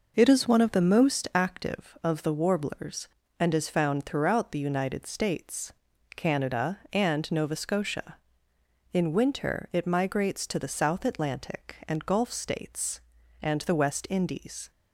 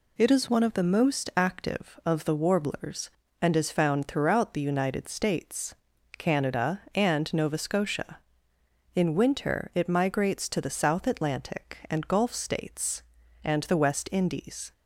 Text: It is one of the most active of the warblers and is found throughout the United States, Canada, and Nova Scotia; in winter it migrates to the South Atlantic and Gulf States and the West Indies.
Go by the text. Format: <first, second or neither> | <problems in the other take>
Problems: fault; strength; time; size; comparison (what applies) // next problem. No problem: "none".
second | starts louder than the rest; noticeable; until 1.5 s; 5.5 dB